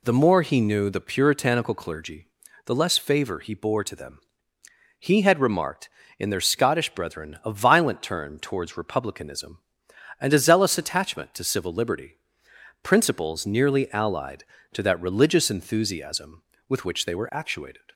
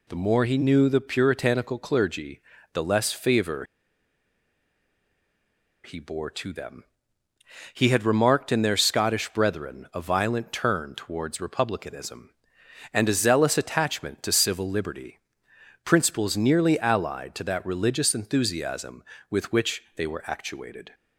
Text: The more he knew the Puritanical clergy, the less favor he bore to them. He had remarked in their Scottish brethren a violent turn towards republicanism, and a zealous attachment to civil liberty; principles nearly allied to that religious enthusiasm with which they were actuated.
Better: first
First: none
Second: pauses between "favor" and "he"; strong; at 3.6 s; 2.1 s long

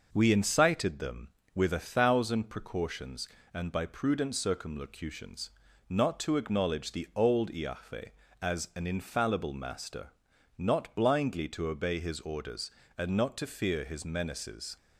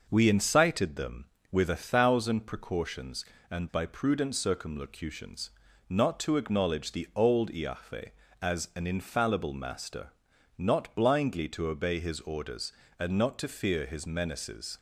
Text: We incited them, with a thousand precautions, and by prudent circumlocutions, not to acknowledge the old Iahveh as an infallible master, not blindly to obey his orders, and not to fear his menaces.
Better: neither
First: none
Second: none

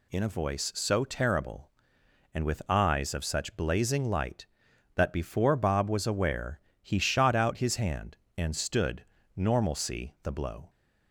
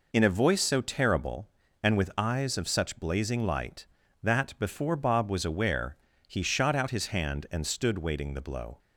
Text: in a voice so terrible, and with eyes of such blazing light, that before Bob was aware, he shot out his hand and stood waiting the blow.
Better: second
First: says "normalcy" for "waiting"; at 9.3 s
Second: none

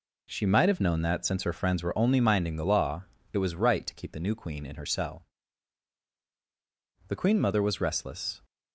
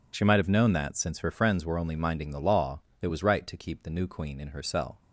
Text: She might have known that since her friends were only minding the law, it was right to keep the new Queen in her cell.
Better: second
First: goes on to say "The Queen Mother was restless"; from 7.0 s on; 1.3 s long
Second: none

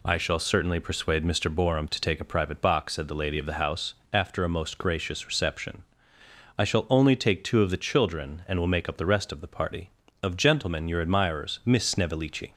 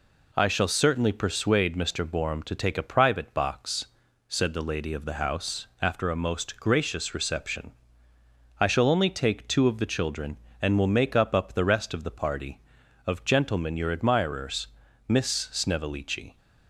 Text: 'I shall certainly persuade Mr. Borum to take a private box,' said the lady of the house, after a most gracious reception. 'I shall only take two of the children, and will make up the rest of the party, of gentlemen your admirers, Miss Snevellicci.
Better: first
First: none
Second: says "up" twice; at 11.3 s

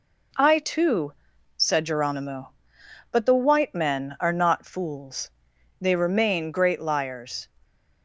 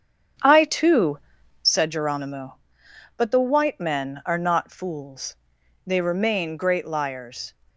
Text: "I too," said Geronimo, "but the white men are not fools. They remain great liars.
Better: first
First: none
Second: starts louder than the rest; strong; until 1.9 s; 8 dB

